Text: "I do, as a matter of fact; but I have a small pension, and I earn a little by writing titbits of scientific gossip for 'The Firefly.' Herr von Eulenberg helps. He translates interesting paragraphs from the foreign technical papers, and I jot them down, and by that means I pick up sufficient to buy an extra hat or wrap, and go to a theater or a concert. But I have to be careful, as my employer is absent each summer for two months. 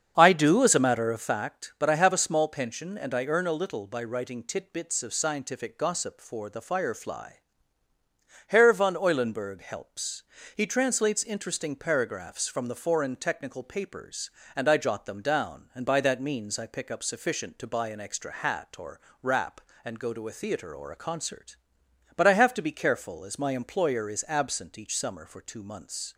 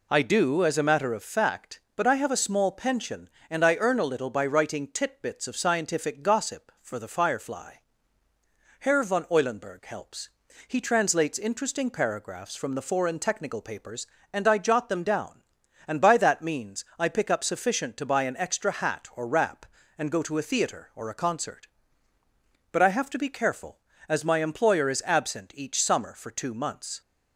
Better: second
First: starts louder than the rest; strong; until 1.5 s; 7.5 dB // pauses between "or" and "wrap"; slight; at 18.9 s; 0.20 s long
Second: none

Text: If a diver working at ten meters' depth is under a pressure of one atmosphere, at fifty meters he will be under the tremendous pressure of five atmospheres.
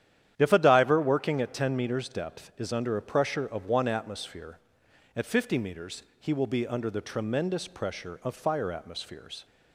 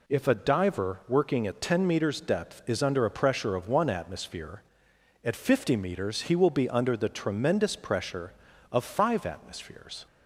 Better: second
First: starts louder than the rest; strong; until 1.3 s; 10.5 dB // pauses between "meters" and "he"; slight; at 6.0 s; 0.16 s long // says "fire" for "five"; at 8.3 s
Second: none

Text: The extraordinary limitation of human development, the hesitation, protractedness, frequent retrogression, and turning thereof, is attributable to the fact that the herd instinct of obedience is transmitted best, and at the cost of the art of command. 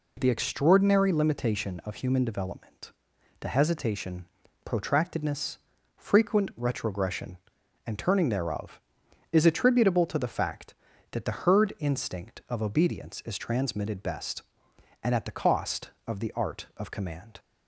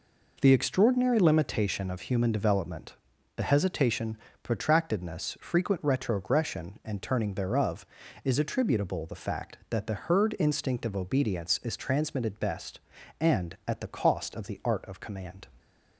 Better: first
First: none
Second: skips "to"; at 9.0 s

